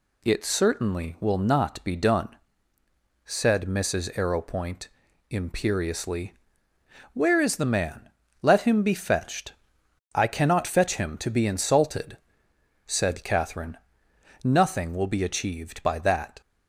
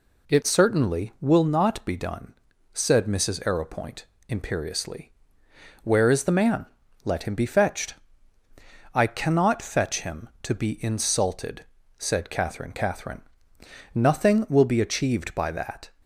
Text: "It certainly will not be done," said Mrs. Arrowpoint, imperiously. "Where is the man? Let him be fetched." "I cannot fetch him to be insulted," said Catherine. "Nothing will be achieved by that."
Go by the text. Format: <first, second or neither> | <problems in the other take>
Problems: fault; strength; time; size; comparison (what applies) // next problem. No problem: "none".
first | says "Catherine" twice; at 12.7 s